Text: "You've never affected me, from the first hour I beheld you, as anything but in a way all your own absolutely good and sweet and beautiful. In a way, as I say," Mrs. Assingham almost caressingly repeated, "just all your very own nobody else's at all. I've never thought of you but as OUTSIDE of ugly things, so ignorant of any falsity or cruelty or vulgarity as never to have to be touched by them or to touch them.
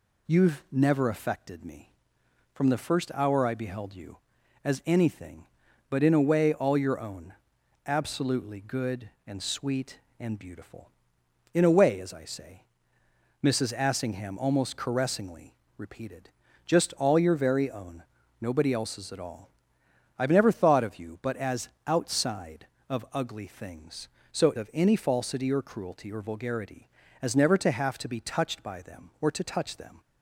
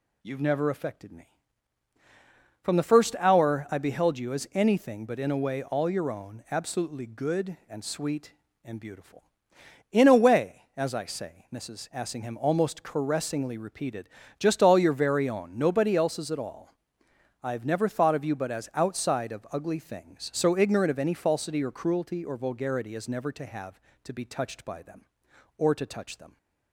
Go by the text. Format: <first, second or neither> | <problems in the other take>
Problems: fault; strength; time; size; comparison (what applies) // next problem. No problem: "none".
second | pauses between "own" and "absolutely"; noticeable; at 7.3 s; 0.52 s long // pauses between "caressingly" and "repeated"; slight; at 15.5 s; 0.24 s long // pauses between "own" and "nobody"; at 18.0 s; 0.40 s long // pauses between "as" and "OUTSIDE"; slight; at 21.6 s; 0.16 s long // skips "ignorant"; at 24.5 s